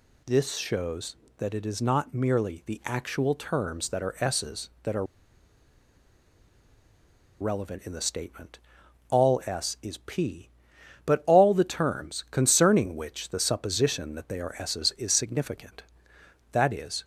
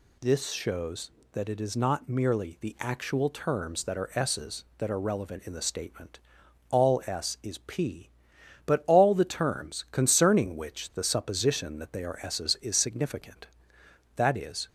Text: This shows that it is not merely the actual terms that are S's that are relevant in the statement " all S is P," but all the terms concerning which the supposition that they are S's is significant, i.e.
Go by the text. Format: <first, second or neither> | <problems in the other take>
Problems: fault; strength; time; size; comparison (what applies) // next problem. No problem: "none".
second | pauses between "are" and "relevant"; strong; at 5.0 s; 2.3 s long